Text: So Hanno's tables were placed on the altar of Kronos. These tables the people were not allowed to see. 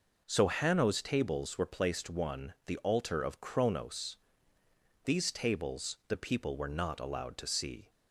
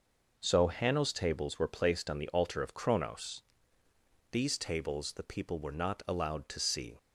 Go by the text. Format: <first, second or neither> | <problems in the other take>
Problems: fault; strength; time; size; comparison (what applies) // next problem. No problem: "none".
second | says "one" for "on"; at 2.0 s